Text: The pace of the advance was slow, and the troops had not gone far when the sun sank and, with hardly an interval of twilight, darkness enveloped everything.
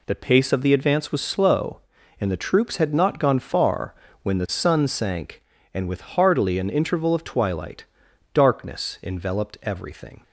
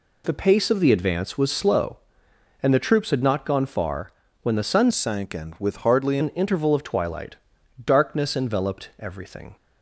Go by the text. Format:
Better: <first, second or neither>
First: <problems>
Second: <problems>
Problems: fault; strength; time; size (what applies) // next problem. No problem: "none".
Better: first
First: pauses between "far" and "when"; slight; at 3.9 s; 0.28 s long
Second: pauses between "far" and "when"; slight; at 4.0 s; 0.32 s long // changes voice from "sank" to "hardly"; from 4.9 to 6.1 s; 1.2 s long